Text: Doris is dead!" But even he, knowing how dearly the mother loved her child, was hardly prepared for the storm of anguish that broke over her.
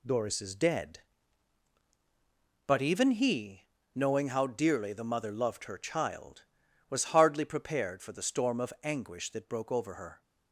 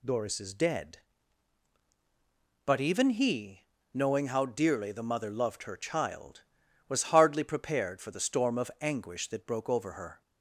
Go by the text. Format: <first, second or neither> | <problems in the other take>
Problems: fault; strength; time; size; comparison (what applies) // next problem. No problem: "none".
second | gets quieter; noticeable; throughout; 6 dB